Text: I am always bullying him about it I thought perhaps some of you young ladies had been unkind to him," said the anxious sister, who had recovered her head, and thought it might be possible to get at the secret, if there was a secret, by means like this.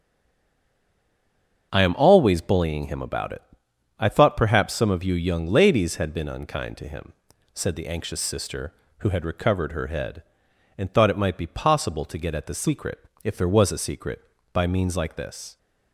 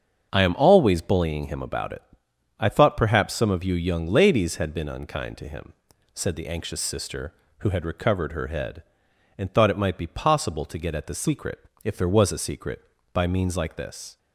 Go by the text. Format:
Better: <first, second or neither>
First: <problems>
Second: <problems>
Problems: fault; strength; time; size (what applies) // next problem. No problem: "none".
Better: second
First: stays silent before the first word; noticeable; until 1.7 s; 1.7 s long // starts louder than the rest; strong; until 2.7 s; 7.5 dB // pauses between "it" and "I"; noticeable; at 3.4 s; 0.58 s long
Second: starts louder than the rest; strong; until 1.3 s; 7.5 dB // pauses between "it" and "I"; noticeable; at 2.0 s; 0.58 s long